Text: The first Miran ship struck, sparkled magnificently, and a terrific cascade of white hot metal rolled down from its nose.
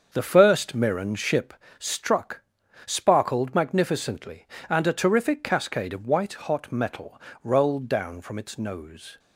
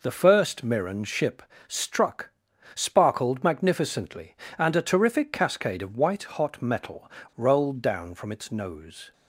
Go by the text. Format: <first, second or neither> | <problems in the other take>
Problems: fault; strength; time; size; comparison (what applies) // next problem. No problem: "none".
second | starts louder than the rest; until 1.6 s; 7 dB // pauses between "ship" and "struck"; slight; at 1.5 s; 0.24 s long; slight in the second // pauses between "metal" and "rolled"; slight; at 7.2 s; 0.22 s long; slight in the second